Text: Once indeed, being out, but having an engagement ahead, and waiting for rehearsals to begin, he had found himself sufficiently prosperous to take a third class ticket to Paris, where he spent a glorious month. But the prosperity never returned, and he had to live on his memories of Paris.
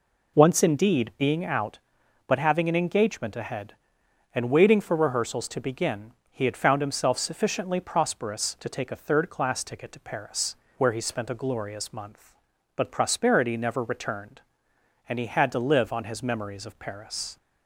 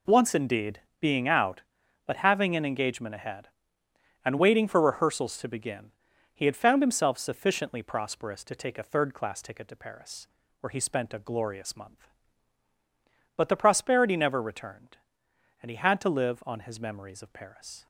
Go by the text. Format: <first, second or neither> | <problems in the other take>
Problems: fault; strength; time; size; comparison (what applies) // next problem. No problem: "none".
second | skips "the"; at 12.8 s